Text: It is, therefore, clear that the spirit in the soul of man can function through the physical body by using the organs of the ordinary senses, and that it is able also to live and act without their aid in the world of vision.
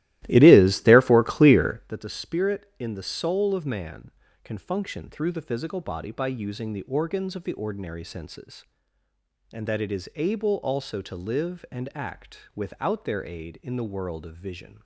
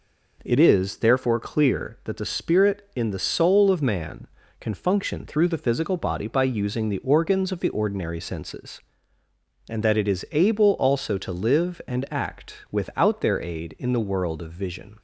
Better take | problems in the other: second | starts louder than the rest; strong; until 2.0 s; 16 dB

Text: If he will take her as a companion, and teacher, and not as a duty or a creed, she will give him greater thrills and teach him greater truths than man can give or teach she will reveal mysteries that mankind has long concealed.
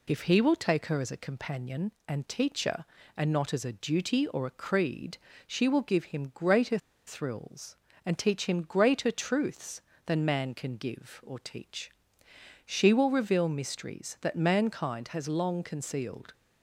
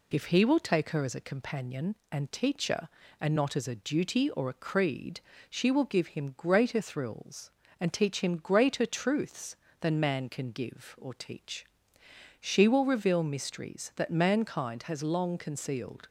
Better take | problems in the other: second | pauses between "greater" and "thrills"; slight; at 6.7 s; 0.28 s long // pauses between "teach" and "she"; noticeable; at 11.8 s; 0.78 s long; noticeable in the second

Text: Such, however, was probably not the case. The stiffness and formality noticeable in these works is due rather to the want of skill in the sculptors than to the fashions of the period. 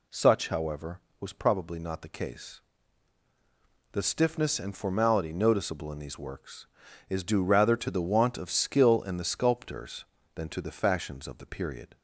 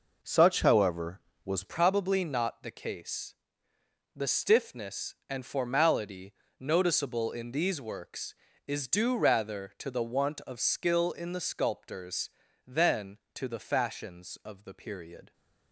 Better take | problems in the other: first | changes voice at "probably"; from 1.6 s on; 13.7 s long // pauses between "formality" and "noticeable"; slight; at 6.3 s; 0.26 s long

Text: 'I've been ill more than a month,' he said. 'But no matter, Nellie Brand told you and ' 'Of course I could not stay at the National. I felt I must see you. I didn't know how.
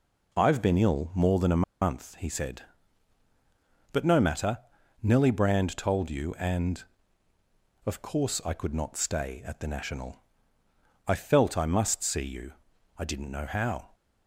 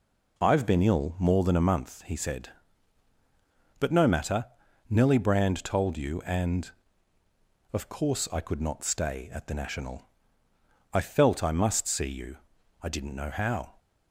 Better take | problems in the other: second | pauses between "a" and "month"; slight; at 1.6 s; 0.19 s long

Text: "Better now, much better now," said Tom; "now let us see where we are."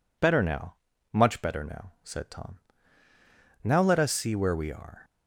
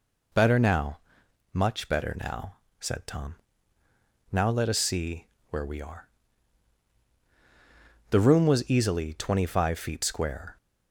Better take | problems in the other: first | pauses between "see" and "where"; slight; at 5.2 s; 0.24 s long // goes on to say "The room was easily twenty five feet square"; strong; from 8.0 s on; 2.4 s long

